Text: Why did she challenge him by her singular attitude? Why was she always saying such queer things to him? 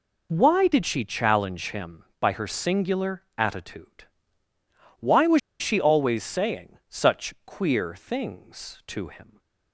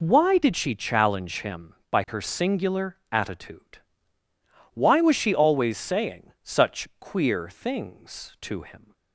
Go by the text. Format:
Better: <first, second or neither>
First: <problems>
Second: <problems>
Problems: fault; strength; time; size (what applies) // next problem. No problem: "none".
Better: second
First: pauses between "was" and "she"; slight; at 5.3 s; 0.20 s long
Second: none